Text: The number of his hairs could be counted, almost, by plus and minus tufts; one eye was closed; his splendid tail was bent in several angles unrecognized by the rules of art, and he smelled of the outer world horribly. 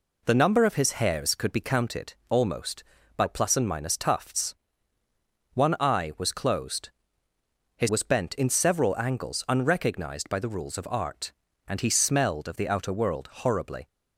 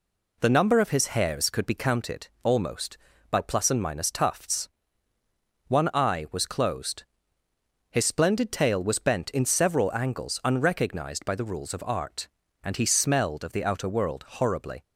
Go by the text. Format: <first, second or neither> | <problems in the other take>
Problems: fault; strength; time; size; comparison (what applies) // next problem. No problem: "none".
second | skips "splendid tail"; at 7.8 s